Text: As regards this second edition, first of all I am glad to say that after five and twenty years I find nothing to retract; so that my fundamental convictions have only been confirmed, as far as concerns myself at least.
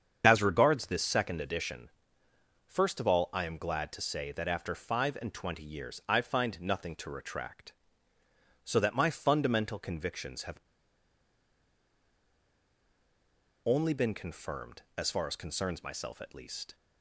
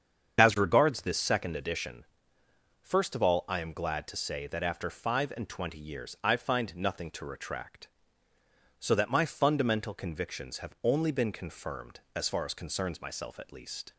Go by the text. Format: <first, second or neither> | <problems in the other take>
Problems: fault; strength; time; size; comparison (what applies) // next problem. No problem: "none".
second | starts louder than the rest; strong; until 1.2 s; 7.5 dB; strong in the second // pauses between "have" and "only"; strong; at 10.5 s; 3.0 s long